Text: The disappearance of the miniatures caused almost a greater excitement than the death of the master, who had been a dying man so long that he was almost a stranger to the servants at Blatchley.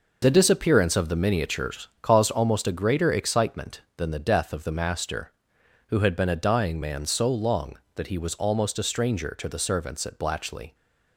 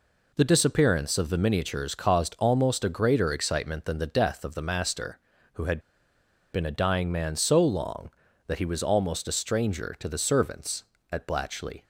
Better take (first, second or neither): first